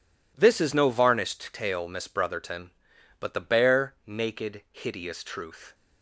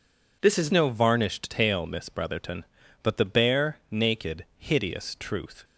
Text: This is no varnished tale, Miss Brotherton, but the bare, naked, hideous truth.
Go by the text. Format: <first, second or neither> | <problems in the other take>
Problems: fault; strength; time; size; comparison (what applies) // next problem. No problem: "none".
first | changes voice at "no"; from 0.7 s on; 4.9 s long